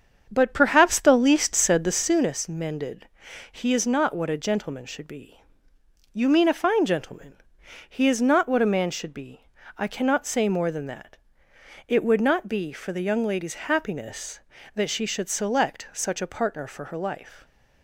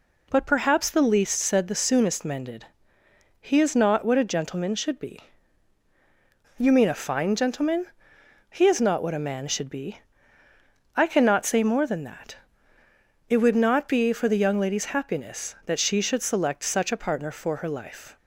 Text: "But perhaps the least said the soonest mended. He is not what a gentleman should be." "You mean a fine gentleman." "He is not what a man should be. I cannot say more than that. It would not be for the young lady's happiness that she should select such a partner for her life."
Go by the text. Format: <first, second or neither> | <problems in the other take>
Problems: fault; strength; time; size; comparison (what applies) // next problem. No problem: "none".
second | starts louder than the rest; strong; until 2.2 s; 7.5 dB